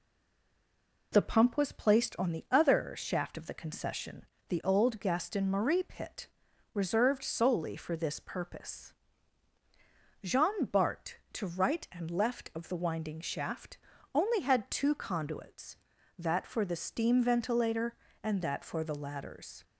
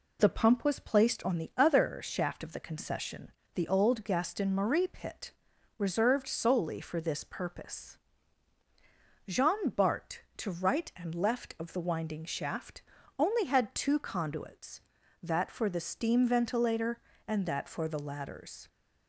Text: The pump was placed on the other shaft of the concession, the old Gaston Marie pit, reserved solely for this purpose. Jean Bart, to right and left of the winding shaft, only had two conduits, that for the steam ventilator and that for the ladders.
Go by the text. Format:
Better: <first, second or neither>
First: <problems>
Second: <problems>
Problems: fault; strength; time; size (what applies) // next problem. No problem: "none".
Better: second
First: stays silent before the first word; until 1.1 s; 1.1 s long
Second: none